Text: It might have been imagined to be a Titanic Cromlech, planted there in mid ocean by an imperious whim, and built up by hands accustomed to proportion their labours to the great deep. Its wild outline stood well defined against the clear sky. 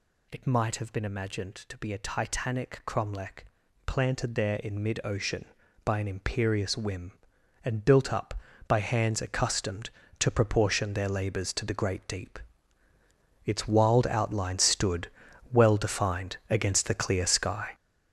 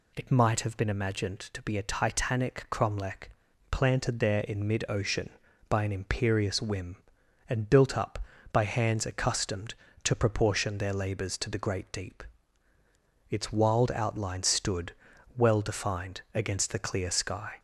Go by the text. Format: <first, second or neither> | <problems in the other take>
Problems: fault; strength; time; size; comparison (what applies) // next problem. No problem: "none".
second | gets louder; strong; throughout; 9 dB // pauses between "stood" and "well"; at 15.0 s; 0.42 s long; also in the second